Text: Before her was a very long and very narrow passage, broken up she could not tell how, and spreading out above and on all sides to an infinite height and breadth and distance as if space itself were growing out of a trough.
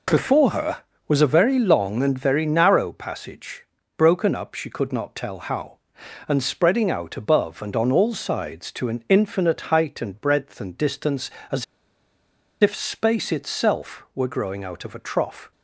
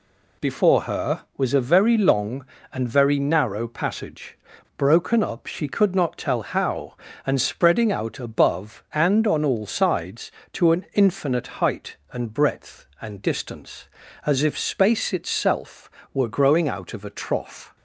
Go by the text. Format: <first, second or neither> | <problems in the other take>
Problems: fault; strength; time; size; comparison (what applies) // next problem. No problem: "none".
second | pauses between "as" and "if"; at 11.6 s; 0.98 s long